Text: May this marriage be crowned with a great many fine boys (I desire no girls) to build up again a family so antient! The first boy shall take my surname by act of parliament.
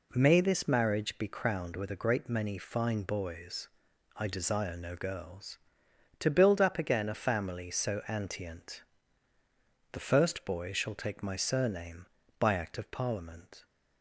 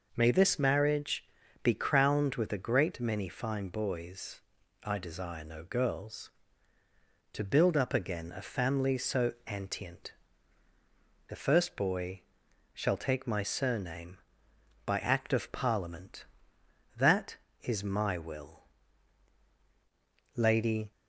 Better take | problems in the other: first | pauses between "marriage" and "be"; at 1.2 s; 0.38 s long // pauses between "boy" and "shall"; noticeable; at 12.2 s; 0.52 s long // goes on to say "That is my will Lady"; strong; from 16.9 s on; 3.9 s long

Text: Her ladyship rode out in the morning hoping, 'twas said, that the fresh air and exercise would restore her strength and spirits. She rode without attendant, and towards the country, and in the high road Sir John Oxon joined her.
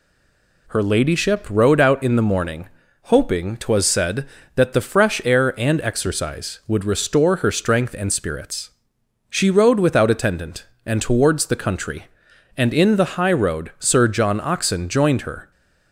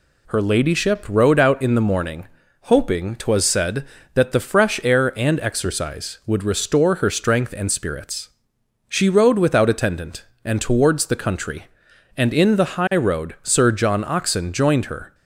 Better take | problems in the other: second | stays silent before the first word; slight; until 0.6 s; 0.6 s long // pauses between "morning" and "hoping"; slight; at 2.6 s; 0.36 s long; slight in the second

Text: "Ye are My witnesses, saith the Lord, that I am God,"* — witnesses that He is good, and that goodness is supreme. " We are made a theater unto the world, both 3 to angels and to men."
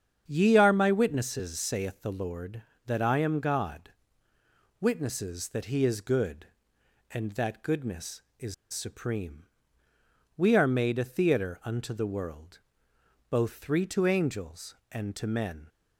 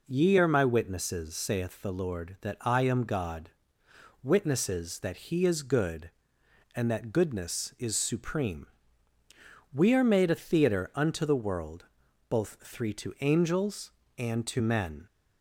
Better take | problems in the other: second | starts louder than the rest; strong; until 1.2 s; 8.5 dB // pauses between "is" and "supreme"; slight; at 8.5 s; 0.18 s long

